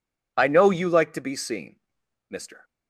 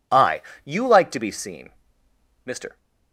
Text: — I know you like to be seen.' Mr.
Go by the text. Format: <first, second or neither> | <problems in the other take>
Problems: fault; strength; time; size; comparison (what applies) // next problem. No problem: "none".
first | skips "know"; at 0.5 s